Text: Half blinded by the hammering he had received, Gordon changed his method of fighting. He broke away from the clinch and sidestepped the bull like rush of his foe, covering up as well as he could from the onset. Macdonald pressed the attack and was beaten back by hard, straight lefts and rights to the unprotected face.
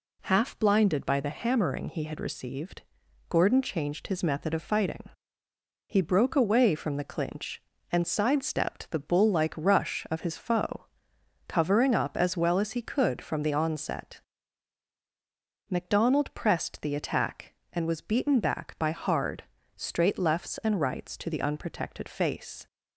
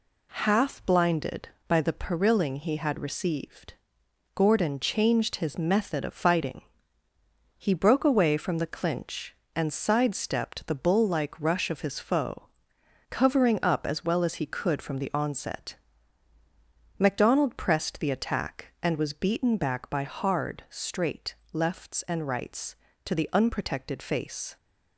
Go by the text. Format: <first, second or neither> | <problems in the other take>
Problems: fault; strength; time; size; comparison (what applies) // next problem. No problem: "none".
first | says "perilling" for "hammering"; at 1.9 s // pauses between "straight" and "lefts"; slight; at 21.3 s; 0.18 s long